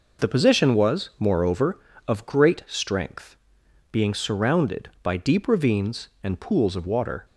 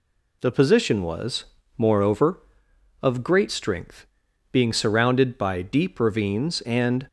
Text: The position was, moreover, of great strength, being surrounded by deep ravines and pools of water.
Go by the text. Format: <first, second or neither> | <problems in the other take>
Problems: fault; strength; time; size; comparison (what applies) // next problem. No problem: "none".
first | stops before "pools of water"; at 7.0 s